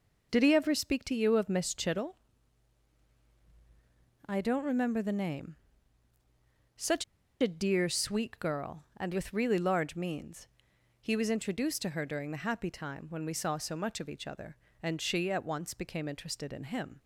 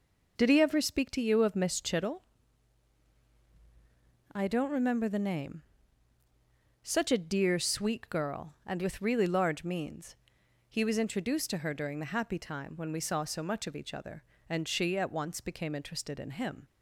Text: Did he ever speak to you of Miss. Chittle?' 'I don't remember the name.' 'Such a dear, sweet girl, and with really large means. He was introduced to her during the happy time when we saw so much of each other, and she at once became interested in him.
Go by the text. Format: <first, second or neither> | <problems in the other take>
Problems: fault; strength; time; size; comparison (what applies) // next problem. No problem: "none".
second | pauses between "Such" and "a"; at 7.0 s; 0.36 s long